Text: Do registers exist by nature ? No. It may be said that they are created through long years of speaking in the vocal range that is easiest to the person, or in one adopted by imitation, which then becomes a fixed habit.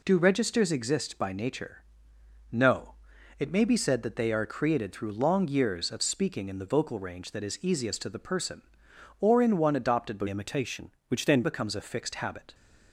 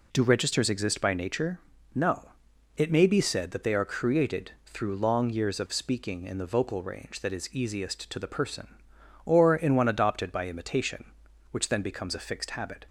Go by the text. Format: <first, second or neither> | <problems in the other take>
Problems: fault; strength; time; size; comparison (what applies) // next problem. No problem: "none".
second | changes voice from "imitation" to "then"; from 10.2 to 11.4 s; 1.2 s long